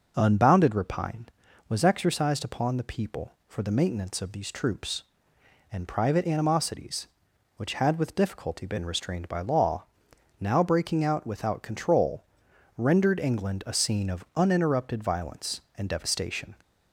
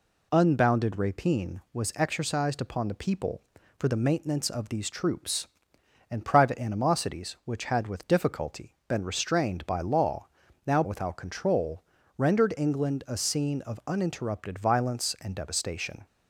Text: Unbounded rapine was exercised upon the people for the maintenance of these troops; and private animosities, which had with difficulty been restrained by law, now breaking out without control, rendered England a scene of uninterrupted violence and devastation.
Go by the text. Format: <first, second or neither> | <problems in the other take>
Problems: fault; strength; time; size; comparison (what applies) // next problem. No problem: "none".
first | skips "breaking out"; at 10.8 s